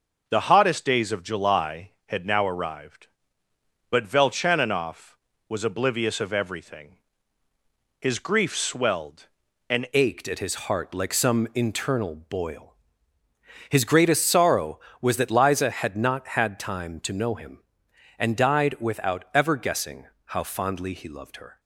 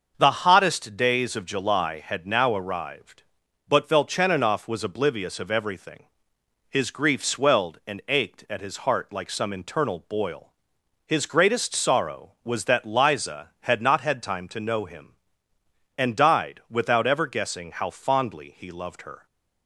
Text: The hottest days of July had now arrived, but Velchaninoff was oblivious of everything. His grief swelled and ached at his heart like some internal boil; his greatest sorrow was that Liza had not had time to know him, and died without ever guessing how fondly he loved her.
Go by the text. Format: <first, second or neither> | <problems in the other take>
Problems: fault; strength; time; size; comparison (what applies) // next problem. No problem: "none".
second | starts louder than the rest; until 1.2 s; 6 dB; also in the second // changes voice at "ached"; from 9.9 s on; 11.6 s long // pauses between "guessing" and "how"; slight; at 20.0 s; 0.22 s long